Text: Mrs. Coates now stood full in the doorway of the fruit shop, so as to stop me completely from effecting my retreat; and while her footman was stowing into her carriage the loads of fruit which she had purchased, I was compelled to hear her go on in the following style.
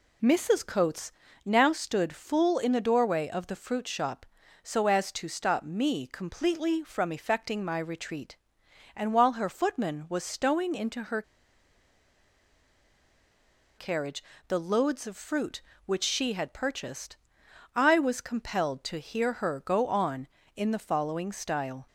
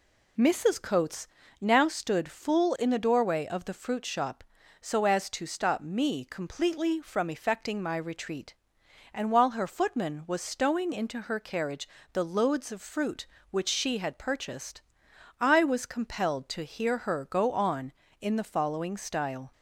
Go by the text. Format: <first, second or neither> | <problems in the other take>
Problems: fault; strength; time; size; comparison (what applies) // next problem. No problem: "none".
second | pauses between "Coates" and "now"; slight; at 1.1 s; 0.34 s long; slight in the second // pauses between "her" and "carriage"; strong; at 11.2 s; 2.5 s long // pauses between "carriage" and "the"; slight; at 14.2 s; 0.24 s long; slight in the second